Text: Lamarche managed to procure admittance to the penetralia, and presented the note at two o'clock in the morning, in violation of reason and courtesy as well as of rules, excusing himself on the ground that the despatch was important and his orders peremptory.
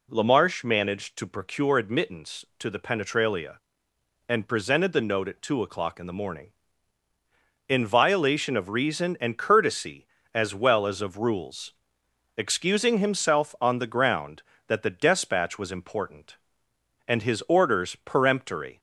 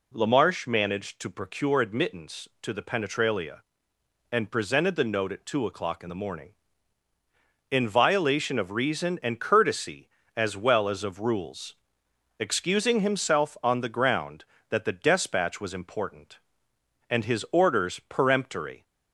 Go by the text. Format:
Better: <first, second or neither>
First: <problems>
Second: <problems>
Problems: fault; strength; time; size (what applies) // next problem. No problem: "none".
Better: neither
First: none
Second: none